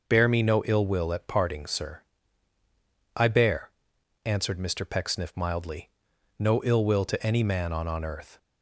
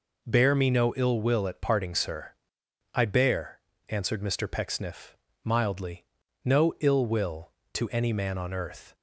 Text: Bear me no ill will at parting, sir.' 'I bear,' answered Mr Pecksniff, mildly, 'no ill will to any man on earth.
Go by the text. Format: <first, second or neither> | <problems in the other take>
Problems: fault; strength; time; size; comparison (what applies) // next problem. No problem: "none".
second | says "on" twice; at 7.8 s